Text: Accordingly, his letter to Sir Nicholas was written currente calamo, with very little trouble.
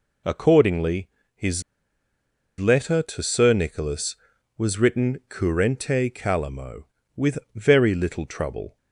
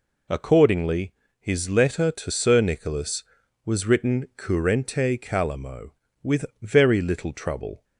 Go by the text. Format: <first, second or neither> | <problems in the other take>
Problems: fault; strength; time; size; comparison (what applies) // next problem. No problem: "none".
second | pauses between "his" and "letter"; at 1.6 s; 0.98 s long // pauses between "with" and "very"; slight; at 7.3 s; 0.16 s long; slight in the second